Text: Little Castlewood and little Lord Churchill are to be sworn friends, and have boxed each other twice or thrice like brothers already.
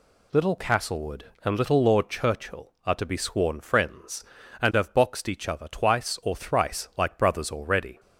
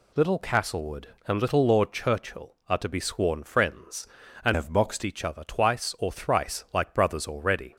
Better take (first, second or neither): first